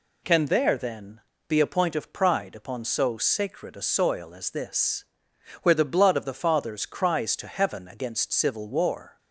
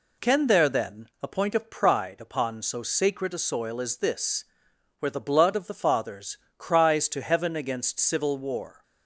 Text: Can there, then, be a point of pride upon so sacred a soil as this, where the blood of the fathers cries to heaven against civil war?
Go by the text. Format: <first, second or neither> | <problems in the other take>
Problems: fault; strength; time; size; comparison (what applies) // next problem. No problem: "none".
first | skips "be"; at 1.1 s // pauses between "fathers" and "cries"; slight; at 6.3 s; 0.20 s long